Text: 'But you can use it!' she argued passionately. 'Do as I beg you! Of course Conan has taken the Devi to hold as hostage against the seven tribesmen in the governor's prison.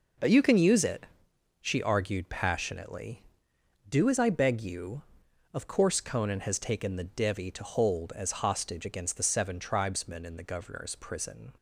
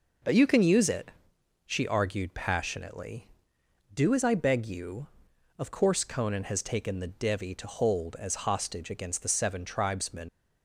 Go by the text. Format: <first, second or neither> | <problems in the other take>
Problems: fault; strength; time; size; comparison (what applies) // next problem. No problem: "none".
first | stops before "in the governor's prison"; at 10.2 s